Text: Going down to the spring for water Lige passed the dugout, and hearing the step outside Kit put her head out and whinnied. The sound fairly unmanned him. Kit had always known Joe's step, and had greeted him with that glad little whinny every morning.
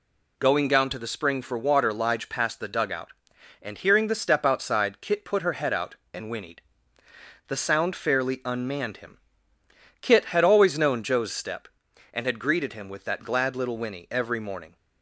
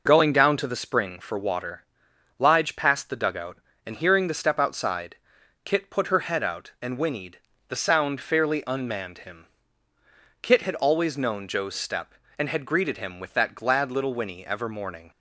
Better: first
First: none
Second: pauses between "water" and "Lige"; noticeable; at 1.8 s; 0.56 s long // pauses between "outside" and "Kit"; noticeable; at 5.1 s; 0.48 s long // says "ever" for "every"; at 14.4 s

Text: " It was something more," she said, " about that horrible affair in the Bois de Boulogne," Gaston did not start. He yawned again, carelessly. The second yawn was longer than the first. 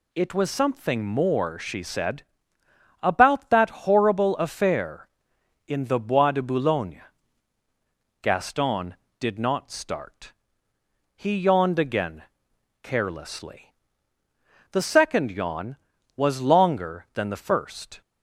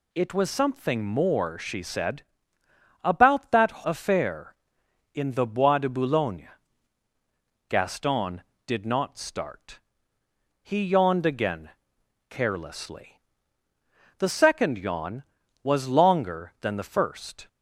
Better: first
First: none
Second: skips "horrible"; at 3.8 s

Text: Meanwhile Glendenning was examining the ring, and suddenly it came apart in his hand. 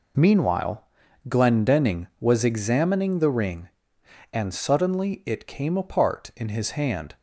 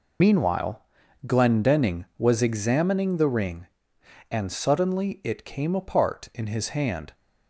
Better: first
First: pauses between "Meanwhile" and "Glendenning"; noticeable; at 0.8 s; 0.46 s long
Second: loses the start of "Meanwhile"; at 0.2 s; 70 ms // pauses between "Meanwhile" and "Glendenning"; noticeable; at 0.7 s; 0.46 s long

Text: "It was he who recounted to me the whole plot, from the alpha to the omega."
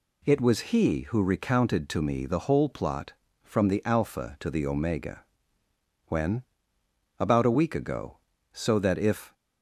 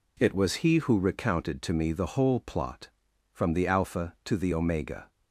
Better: second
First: goes on to say "When About a week ago so that if"; strong; from 6.0 s on; 3.2 s long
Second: none

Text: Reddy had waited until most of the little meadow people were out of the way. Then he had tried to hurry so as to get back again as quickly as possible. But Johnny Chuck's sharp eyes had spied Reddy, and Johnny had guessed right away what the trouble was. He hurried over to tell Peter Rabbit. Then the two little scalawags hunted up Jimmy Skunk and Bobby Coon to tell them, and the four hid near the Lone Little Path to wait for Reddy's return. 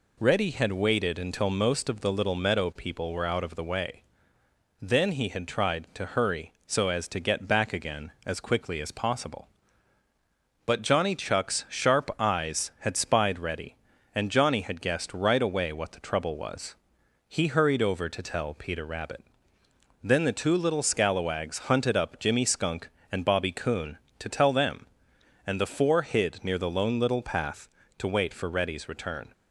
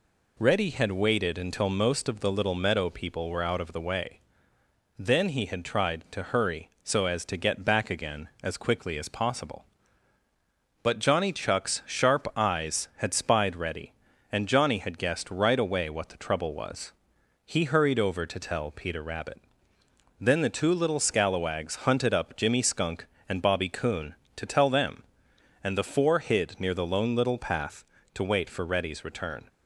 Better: neither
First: none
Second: none

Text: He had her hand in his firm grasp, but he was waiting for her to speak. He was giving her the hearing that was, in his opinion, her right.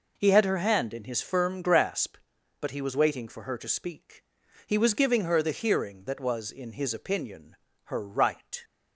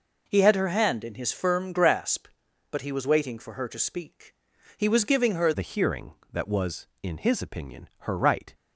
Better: first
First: none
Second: changes voice at "the"; from 5.5 s on; 3.0 s long

